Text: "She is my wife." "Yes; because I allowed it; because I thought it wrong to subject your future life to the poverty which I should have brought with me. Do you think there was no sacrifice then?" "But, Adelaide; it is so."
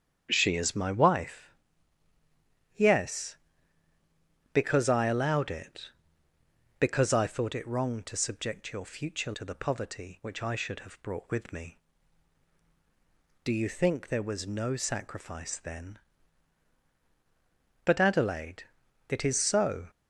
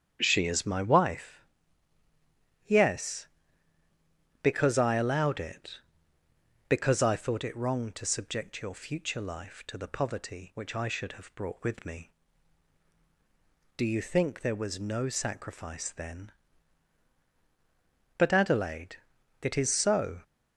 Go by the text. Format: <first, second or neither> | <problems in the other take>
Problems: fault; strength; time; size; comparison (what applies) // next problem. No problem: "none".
second | starts louder than the rest; strong; until 1.3 s; 8.5 dB; strong in the second // skips "life"; at 9.3 s